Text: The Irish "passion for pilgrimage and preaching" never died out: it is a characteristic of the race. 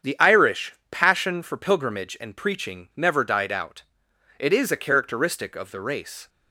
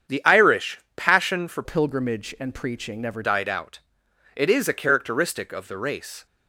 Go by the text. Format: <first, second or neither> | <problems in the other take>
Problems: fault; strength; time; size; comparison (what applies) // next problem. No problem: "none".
first | starts louder than the rest; strong; until 1.3 s; 8 dB; strong in the first // pauses between "Irish" and "passion"; slight; at 0.7 s; 0.18 s long; slight in the first // changes voice from "pilgrimage" to "never"; from 1.6 to 3.2 s; 1.6 s long